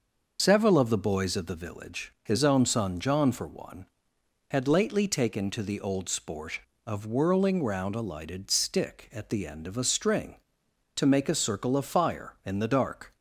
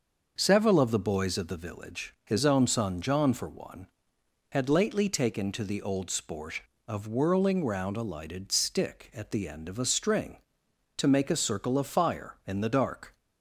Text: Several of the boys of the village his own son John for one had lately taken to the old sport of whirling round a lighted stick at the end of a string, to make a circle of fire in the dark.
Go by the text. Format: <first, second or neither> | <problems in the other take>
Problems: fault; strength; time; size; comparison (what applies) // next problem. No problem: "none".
second | loses the start of "Several"; at 0.3 s; 30 ms // starts louder than the rest; noticeable; until 1.4 s; 6 dB; also in the second